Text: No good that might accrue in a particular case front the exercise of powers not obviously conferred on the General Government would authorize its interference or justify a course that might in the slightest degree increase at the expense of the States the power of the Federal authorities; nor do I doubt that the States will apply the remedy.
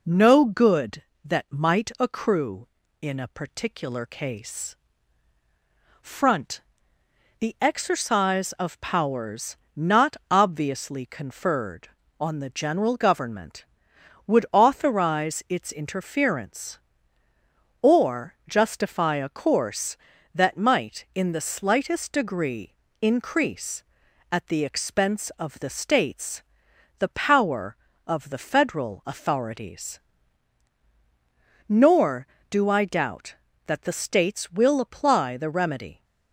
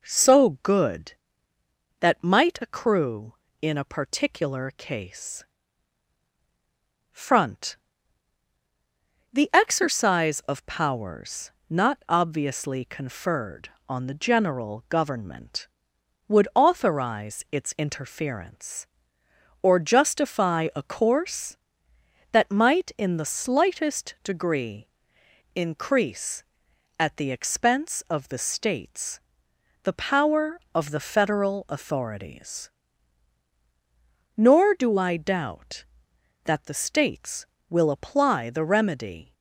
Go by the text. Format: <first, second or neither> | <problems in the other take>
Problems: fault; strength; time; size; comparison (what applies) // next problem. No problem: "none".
first | says "So" for "No"; at 0.0 s // pauses between "case" and "front"; strong; at 5.4 s; 1.6 s long; also in the first // pauses between "front" and "the"; strong; at 7.7 s; 1.5 s long; noticeable in the first // pauses between "powers" and "not"; slight; at 11.5 s; 0.18 s long; slight in the first // pauses between "degree" and "increase"; noticeable; at 24.8 s; 0.66 s long; slight in the first // pauses between "States" and "the"; noticeable; at 29.2 s; 0.64 s long; noticeable in the first